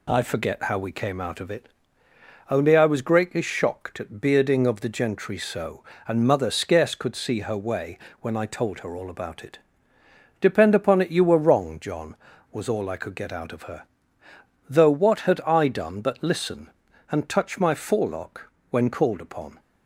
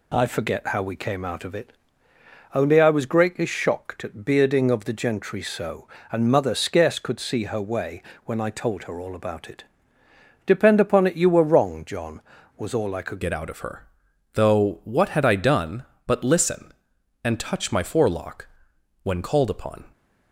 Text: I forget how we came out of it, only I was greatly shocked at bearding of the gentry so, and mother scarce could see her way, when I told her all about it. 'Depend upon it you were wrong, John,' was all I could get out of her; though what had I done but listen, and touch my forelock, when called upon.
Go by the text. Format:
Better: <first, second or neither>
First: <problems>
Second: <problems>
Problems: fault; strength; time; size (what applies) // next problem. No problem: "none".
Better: first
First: none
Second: changes voice at "get"; from 13.2 s on; 6.6 s long